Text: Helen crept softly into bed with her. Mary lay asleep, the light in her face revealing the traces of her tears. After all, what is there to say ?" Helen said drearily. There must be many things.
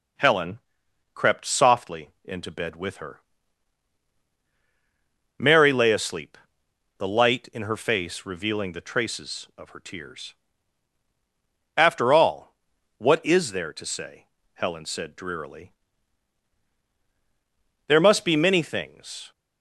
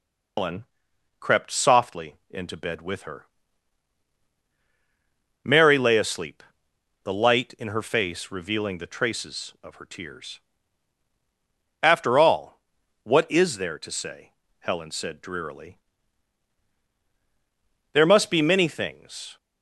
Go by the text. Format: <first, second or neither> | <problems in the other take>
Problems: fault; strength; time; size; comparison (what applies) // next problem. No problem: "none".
first | loses the start of "Helen"; at 0.3 s; 150 ms // pauses between "Helen" and "crept"; noticeable; at 0.6 s; 0.54 s long; noticeable in the first // pauses between "softly" and "into"; slight; at 2.1 s; 0.16 s long; slight in the first